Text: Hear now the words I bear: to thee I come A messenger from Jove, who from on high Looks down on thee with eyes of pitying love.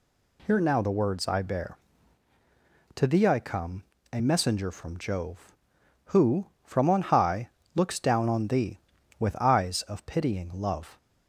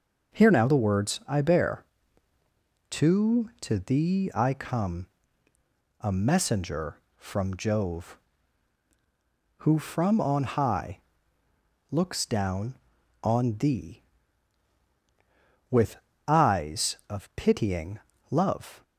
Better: first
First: pauses between "come" and "A"; slight; at 3.8 s; 0.28 s long // pauses between "high" and "Looks"; slight; at 7.4 s; 0.26 s long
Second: says "to" twice; at 3.5 s // pauses between "come" and "A"; noticeable; at 5.0 s; 0.92 s long // pauses between "high" and "Looks"; noticeable; at 10.9 s; 0.88 s long // pauses between "with" and "eyes"; slight; at 15.9 s; 0.28 s long // pauses between "pitying" and "love"; slight; at 18.0 s; 0.28 s long

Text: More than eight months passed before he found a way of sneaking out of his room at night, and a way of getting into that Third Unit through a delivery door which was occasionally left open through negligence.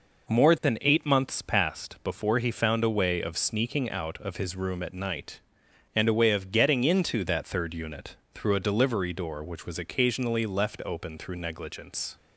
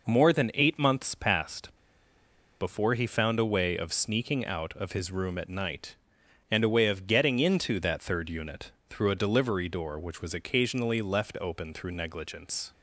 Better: first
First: pauses between "Unit" and "through"; slight; at 8.1 s; 0.18 s long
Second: pauses between "passed" and "before"; noticeable; at 1.7 s; 0.87 s long // pauses between "Unit" and "through"; slight; at 8.6 s; 0.18 s long

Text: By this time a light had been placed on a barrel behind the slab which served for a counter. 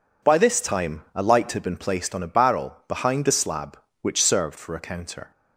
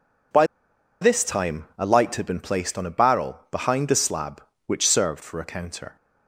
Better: first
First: none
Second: pauses between "By" and "this"; noticeable; at 0.4 s; 0.55 s long

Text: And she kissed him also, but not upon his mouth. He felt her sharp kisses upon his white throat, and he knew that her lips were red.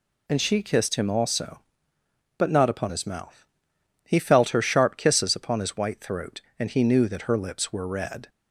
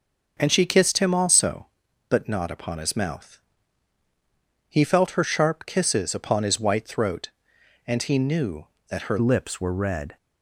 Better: first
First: none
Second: starts louder than the rest; until 1.4 s; 6.5 dB // changes voice at "lips"; from 9.2 s on; 0.9 s long

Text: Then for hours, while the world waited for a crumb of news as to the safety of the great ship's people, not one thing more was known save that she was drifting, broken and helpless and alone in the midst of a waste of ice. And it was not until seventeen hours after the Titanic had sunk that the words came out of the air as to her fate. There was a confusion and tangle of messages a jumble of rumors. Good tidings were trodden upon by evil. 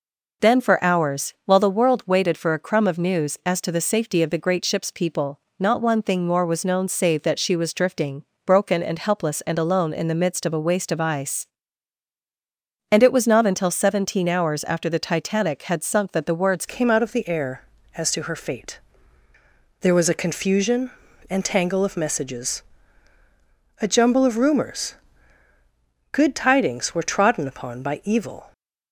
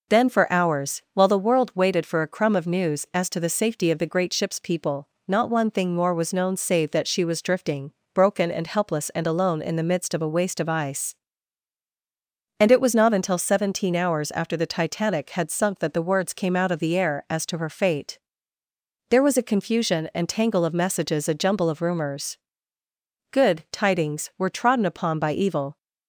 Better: second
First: changes voice at "came"; from 16.6 s on; 11.9 s long // pauses between "messages" and "a"; at 22.6 s; 1.1 s long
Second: none

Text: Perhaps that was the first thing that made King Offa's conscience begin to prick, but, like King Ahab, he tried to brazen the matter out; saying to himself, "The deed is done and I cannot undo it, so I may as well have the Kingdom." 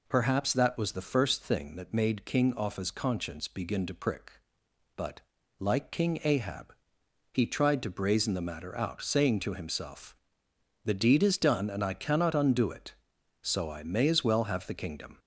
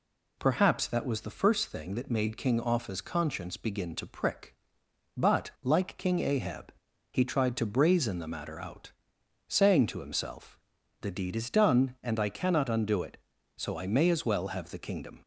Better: neither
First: none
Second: none

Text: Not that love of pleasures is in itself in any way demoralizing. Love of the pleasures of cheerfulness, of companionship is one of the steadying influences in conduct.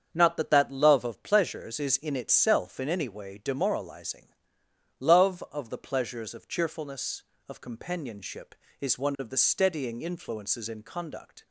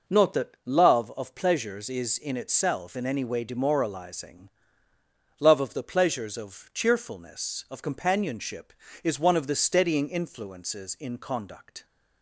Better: second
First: starts louder than the rest; strong; until 1.1 s; 7.5 dB // says "that" twice; at 0.5 s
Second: none

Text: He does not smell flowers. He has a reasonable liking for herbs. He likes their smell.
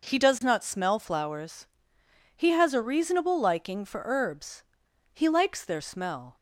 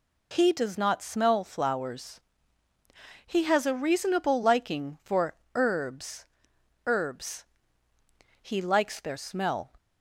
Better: first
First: none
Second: pauses between "for" and "herbs"; slight; at 5.3 s; 0.22 s long // says "herbs" twice; at 6.8 s

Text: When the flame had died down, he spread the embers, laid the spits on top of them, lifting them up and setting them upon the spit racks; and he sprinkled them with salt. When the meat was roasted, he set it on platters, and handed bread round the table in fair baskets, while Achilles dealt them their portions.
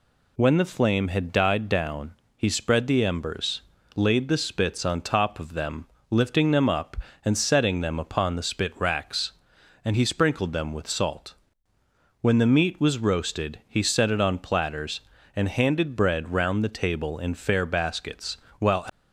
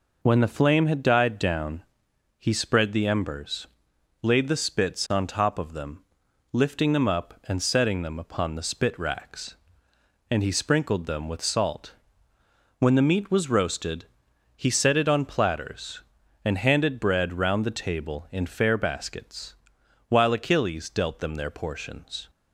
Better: second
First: stops before "Achilles dealt them their portions"; at 18.8 s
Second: none

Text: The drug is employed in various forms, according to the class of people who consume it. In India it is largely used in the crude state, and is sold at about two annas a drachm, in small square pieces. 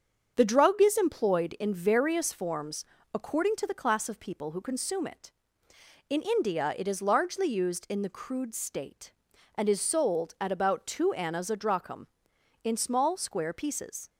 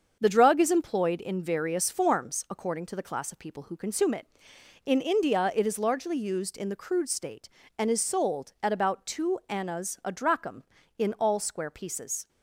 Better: first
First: starts louder than the rest; strong; until 1.3 s; 7.5 dB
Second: starts louder than the rest; until 1.2 s; 7 dB // says "all" for "small"; at 11.1 s

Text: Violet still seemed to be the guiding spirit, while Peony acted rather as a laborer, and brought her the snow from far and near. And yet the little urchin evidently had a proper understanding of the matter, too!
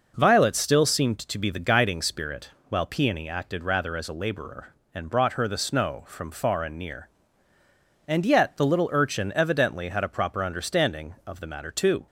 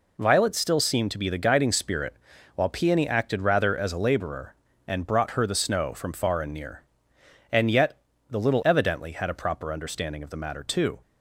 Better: first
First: none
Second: pauses between "yet" and "the"; slight; at 7.9 s; 0.32 s long // skips "urchin"; at 8.6 s

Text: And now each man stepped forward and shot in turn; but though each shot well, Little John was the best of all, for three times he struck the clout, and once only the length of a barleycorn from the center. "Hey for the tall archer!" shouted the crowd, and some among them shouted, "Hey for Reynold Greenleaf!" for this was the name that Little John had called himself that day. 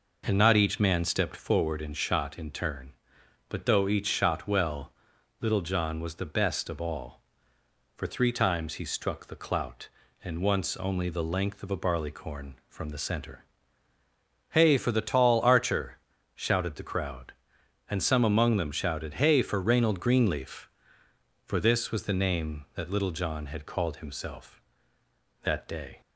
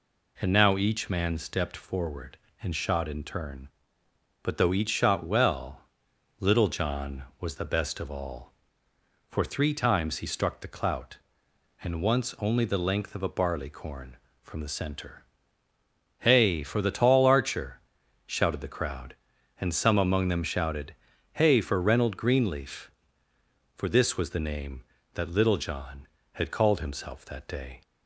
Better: second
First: says "not" for "now"; at 0.3 s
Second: none

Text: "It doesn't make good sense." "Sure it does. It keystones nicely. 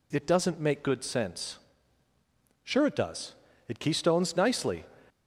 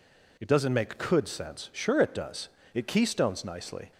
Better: first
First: none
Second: says "could" for "good"; at 0.9 s

